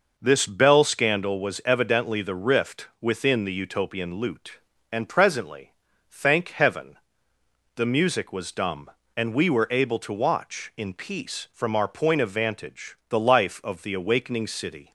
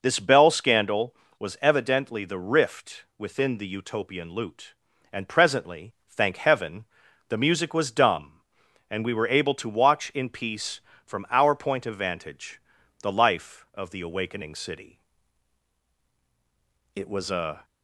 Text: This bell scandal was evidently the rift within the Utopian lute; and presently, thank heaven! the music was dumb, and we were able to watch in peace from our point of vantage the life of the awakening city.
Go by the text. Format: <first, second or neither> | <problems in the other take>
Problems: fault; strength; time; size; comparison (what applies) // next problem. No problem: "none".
first | pauses between "vantage" and "the"; at 12.6 s; 0.42 s long // goes on to say "It was a"; noticeable; from 16.9 s on; 0.70 s long